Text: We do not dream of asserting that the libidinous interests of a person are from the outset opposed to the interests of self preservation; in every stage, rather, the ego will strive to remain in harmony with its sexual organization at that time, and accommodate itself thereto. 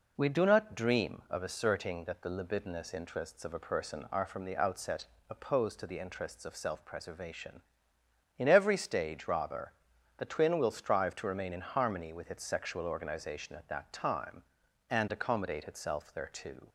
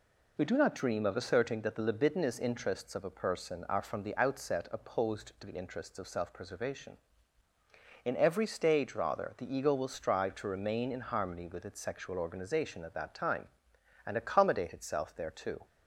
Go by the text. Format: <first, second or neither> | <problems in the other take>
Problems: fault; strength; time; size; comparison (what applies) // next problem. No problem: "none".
second | pauses between "outset" and "opposed"; slight; at 5.0 s; 0.24 s long // says "twin" for "ego"; at 10.2 s